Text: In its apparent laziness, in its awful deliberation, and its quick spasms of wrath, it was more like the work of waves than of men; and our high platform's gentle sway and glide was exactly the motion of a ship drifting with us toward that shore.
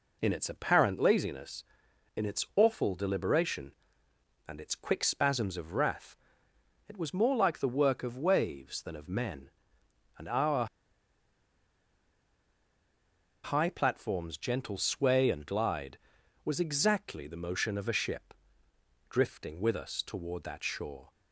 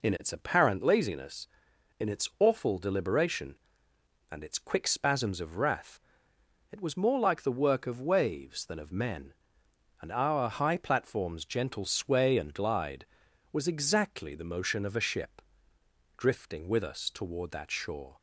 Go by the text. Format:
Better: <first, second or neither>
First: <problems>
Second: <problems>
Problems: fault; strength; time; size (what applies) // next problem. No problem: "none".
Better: second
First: pauses between "our" and "high"; strong; at 10.6 s; 2.7 s long // pauses between "ship" and "drifting"; noticeable; at 18.3 s; 0.76 s long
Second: pauses between "ship" and "drifting"; noticeable; at 15.4 s; 0.76 s long